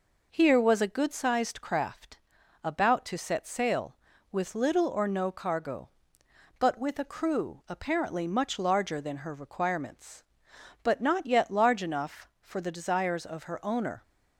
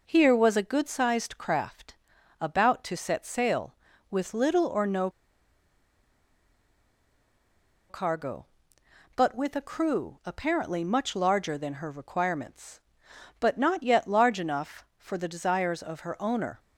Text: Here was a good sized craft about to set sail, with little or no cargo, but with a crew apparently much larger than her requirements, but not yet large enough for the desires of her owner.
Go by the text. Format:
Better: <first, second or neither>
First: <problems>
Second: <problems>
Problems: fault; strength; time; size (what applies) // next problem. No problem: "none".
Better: first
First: pauses between "craft" and "about"; at 2.1 s; 0.44 s long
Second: pauses between "craft" and "about"; at 1.9 s; 0.44 s long // pauses between "no" and "cargo"; strong; at 5.0 s; 2.8 s long